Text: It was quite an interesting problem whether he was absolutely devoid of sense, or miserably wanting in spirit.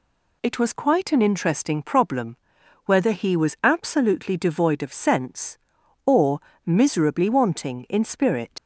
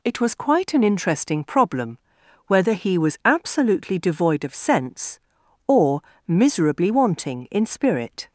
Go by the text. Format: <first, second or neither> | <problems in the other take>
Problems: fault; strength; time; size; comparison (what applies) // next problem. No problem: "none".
second | pauses between "problem" and "whether"; noticeable; at 2.3 s; 0.48 s long; noticeable in the second // pauses between "or" and "miserably"; slight; at 6.3 s; 0.26 s long; slight in the second // leaves "spirit" unfinished; at 8.5 s; 110 ms